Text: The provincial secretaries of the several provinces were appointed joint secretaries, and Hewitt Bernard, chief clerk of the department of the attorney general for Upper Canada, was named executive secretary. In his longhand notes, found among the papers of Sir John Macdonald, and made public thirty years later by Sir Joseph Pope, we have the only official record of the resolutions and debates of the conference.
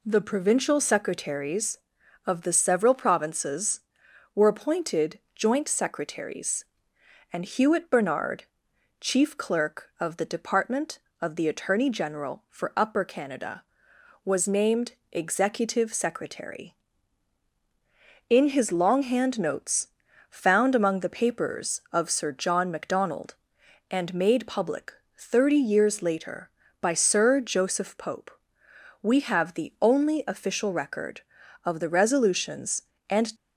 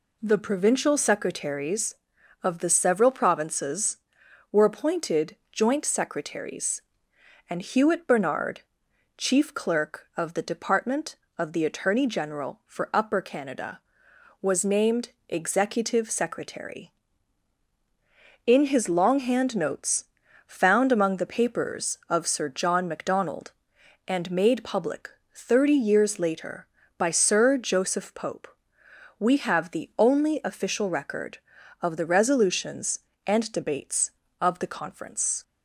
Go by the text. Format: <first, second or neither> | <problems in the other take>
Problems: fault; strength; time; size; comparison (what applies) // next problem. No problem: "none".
second | pauses between "appointed" and "joint"; slight; at 5.1 s; 0.16 s long; slight in the second // pauses between "named" and "executive"; slight; at 14.9 s; 0.18 s long; slight in the second // pauses between "public" and "thirty"; slight; at 24.9 s; 0.22 s long; slight in the second // stops before "debates of the conference"; at 33.3 s